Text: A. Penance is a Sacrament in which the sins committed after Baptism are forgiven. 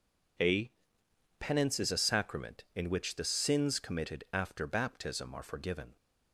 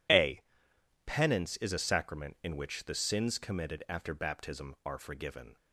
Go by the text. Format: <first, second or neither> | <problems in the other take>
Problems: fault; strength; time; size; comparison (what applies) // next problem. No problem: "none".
neither | none